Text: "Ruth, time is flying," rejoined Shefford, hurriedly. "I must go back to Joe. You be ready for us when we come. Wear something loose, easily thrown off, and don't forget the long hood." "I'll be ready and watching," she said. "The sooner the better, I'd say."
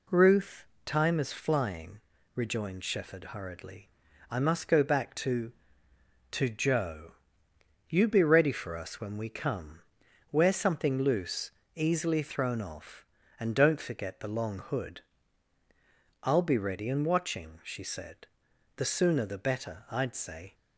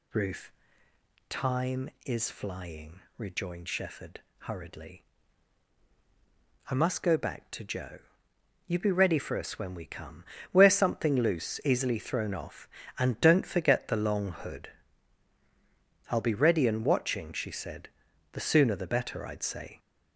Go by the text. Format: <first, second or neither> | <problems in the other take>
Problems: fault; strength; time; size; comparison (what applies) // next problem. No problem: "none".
second | says "to" twice; at 6.3 s